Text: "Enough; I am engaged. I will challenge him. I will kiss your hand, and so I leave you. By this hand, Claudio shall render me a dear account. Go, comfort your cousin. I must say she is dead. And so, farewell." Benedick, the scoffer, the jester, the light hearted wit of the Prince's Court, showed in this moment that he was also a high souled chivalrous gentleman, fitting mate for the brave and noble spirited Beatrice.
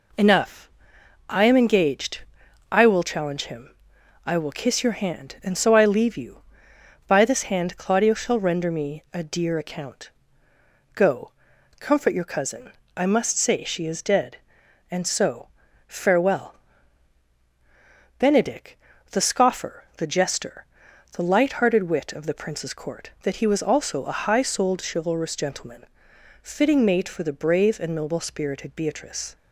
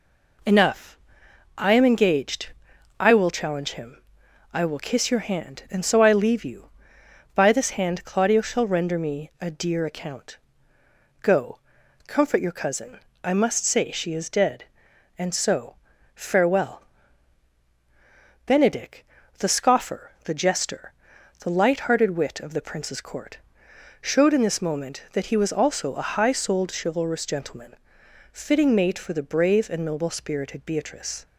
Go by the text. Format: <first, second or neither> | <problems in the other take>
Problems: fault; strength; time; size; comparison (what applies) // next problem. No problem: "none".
second | skips "showed in this moment"; at 23.1 s